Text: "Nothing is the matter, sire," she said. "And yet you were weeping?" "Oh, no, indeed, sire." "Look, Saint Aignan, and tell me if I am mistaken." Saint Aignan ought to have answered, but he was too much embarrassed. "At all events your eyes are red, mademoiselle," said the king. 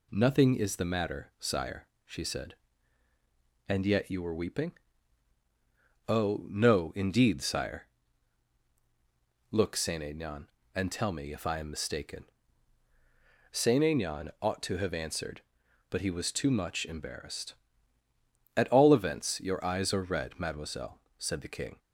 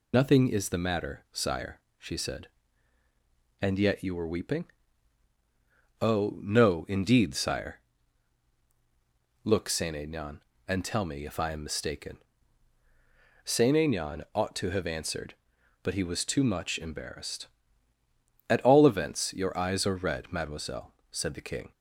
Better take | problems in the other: first | loses the start of "Nothing"; at 0.1 s; 105 ms

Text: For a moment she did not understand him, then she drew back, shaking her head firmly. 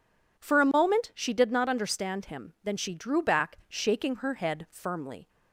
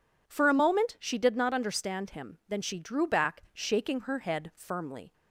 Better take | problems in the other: neither | none

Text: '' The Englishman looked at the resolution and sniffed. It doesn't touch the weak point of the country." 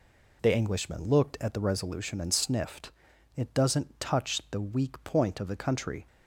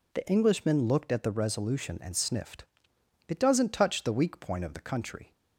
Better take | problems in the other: neither | none

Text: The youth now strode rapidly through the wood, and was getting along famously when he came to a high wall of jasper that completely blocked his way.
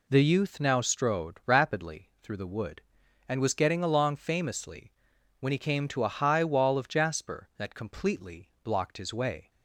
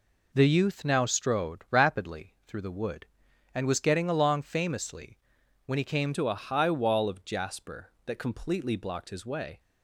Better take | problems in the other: first | pauses between "famously" and "when"; noticeable; at 5.1 s; 0.48 s long; noticeable in the first // changes voice at "to"; from 6.1 s on; 3.4 s long

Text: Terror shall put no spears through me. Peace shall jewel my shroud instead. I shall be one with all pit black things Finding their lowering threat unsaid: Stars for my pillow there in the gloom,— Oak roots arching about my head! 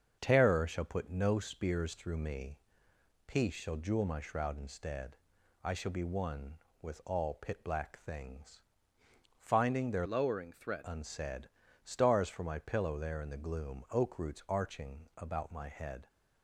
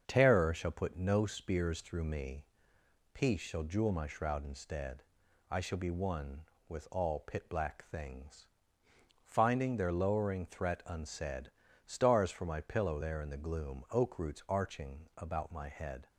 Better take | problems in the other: second | starts louder than the rest; until 1.2 s; 6.5 dB; also in the second // pauses between "things" and "Finding"; noticeable; at 8.6 s; 0.78 s long; noticeable in the second // changes voice from "lowering" to "threat"; from 10.0 to 10.8 s; 0.8 s long

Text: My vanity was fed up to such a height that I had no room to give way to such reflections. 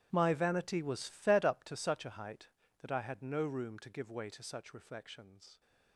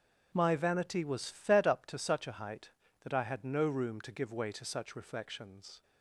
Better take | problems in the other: second | gets quieter; strong; throughout; 18.5 dB // starts louder than the rest; strong; until 1.1 s; 12 dB; strong in the second

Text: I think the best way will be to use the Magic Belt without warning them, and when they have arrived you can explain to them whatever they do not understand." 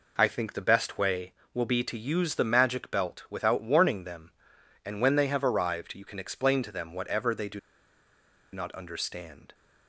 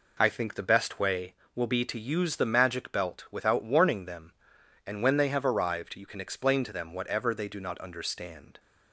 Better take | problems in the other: second | pauses between "do" and "not"; noticeable; at 7.5 s; 0.94 s long

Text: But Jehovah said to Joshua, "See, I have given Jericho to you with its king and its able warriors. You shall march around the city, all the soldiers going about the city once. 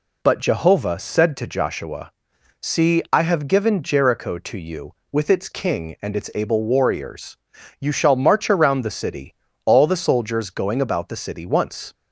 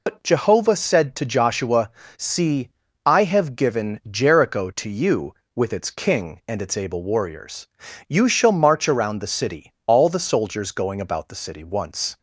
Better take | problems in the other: first | loses the start of "But"; at 0.0 s; 80 ms

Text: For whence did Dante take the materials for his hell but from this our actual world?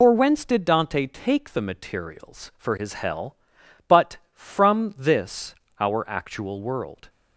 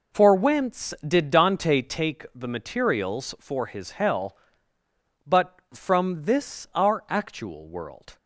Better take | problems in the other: second | loses the start of "For"; at 0.0 s; 105 ms // pauses between "this" and "our"; slight; at 5.5 s; 0.28 s long

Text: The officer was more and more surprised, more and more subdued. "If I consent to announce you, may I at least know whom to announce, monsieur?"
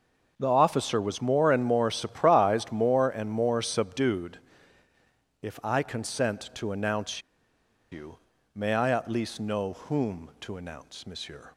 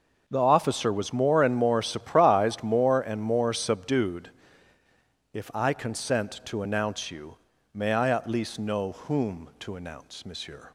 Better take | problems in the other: second | pauses between "announce" and "you"; noticeable; at 7.2 s; 0.70 s long

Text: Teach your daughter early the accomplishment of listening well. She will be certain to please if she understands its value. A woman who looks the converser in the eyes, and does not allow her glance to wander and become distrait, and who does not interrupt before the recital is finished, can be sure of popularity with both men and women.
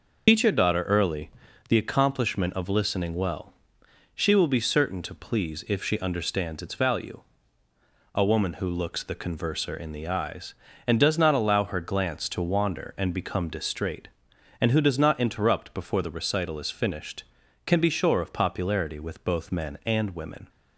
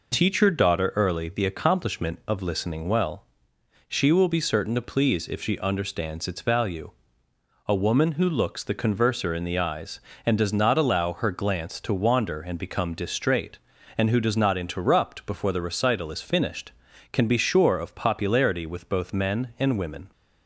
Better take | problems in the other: second | loses the start of "Teach"; at 0.2 s; 85 ms // pauses between "early" and "the"; at 1.2 s; 0.40 s long

